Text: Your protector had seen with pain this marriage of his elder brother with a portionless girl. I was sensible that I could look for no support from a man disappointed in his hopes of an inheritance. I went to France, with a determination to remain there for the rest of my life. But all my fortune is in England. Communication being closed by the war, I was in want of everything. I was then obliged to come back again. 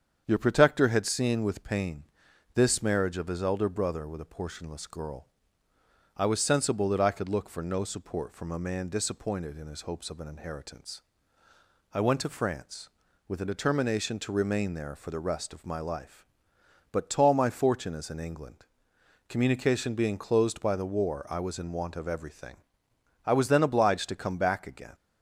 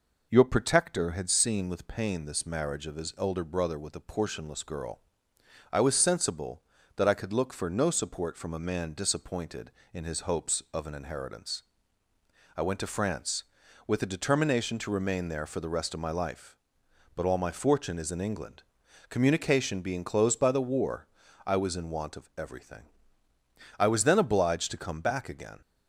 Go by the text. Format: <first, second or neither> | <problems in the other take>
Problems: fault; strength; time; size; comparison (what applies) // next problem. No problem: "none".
second | starts louder than the rest; strong; until 1.2 s; 7.5 dB // pauses between "pain" and "this"; noticeable; at 2.0 s; 0.50 s long // says "tall" for "all"; at 17.1 s